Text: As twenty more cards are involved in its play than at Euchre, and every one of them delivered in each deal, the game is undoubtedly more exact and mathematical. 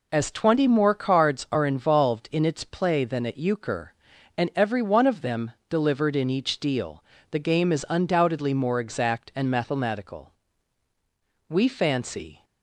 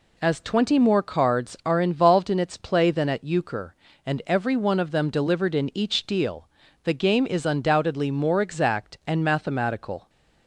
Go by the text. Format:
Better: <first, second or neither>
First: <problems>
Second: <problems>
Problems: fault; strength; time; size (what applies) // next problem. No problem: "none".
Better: second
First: pauses between "them" and "delivered"; slight; at 5.4 s; 0.18 s long // goes on to say "We fancy"; noticeable; from 11.4 s on; 0.94 s long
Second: none